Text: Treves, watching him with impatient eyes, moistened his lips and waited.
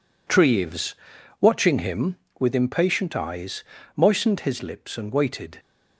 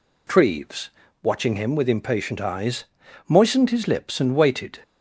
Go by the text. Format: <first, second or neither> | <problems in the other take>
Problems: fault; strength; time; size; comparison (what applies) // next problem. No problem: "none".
neither | none